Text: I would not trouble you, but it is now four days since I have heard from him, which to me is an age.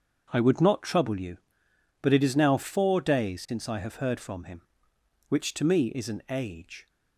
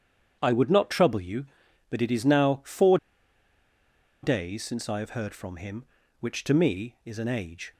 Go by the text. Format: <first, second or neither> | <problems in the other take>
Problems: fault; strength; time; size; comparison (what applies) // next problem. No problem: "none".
first | starts louder than the rest; strong; until 1.4 s; 8 dB; also in the first // pauses between "four" and "days"; strong; at 2.9 s; 1.2 s long